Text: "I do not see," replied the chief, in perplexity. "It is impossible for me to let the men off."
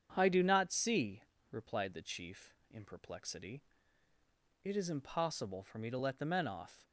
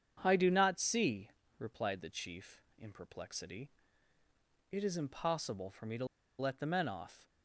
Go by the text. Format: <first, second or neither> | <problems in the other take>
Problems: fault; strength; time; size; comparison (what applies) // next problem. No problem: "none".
first | starts louder than the rest; strong; until 1.2 s; 7.5 dB; strong in the first // pauses between "to" and "let"; slight; at 6.0 s; 0.34 s long